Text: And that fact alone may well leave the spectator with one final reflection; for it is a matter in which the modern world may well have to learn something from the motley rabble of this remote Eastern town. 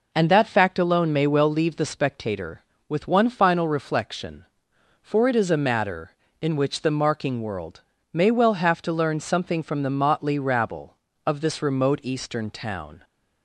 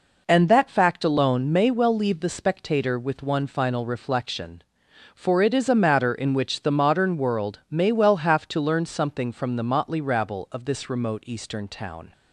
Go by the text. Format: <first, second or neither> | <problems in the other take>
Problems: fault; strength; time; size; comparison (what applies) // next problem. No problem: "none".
second | says "marking" for "modern"; at 6.8 s // pauses between "world" and "may"; slight; at 7.8 s; 0.30 s long